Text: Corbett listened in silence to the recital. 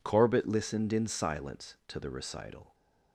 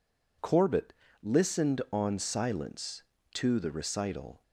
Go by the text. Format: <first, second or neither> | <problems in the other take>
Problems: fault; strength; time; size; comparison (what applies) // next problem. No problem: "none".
first | pauses between "Corbett" and "listened"; slight; at 0.9 s; 0.30 s long // says "on" for "in"; at 1.9 s